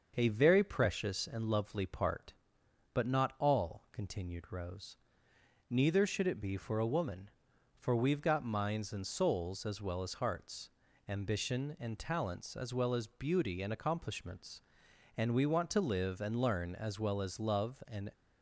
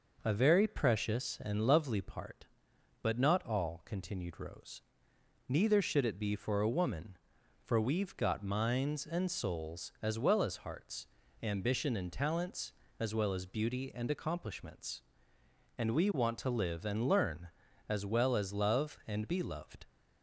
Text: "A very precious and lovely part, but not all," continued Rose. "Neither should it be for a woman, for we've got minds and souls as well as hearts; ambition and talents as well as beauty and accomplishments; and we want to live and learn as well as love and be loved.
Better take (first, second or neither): second